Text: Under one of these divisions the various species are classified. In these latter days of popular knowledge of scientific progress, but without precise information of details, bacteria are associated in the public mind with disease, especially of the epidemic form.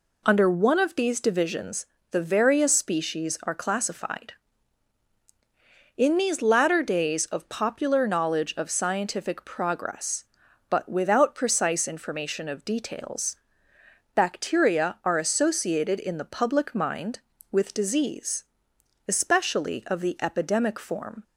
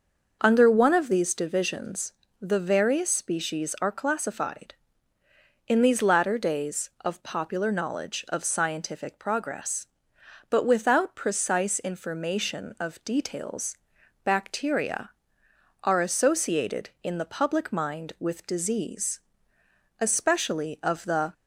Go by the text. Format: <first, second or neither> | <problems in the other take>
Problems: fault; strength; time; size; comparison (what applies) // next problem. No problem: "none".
first | starts louder than the rest; until 1.4 s; 6 dB // pauses between "divisions" and "the"; slight; at 2.1 s; 0.26 s long; slight in the first // stops before "epidemic form"; at 21.3 s